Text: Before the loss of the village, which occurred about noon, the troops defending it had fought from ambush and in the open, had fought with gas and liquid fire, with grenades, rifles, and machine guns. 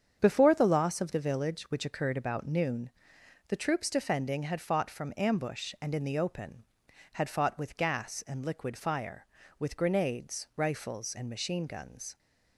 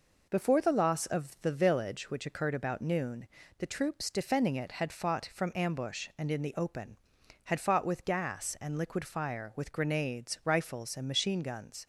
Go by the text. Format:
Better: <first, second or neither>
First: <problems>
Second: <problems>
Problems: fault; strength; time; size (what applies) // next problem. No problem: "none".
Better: second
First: starts louder than the rest; strong; until 1.2 s; 8 dB // skips "it"; at 4.4 s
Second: none